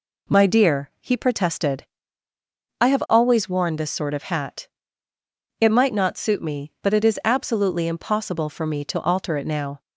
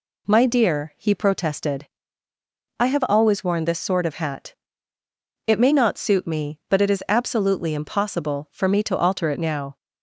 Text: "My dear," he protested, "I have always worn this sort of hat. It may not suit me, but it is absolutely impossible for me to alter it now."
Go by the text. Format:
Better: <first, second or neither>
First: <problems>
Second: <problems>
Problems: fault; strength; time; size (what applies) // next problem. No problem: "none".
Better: second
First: says "might" for "may"; at 5.7 s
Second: none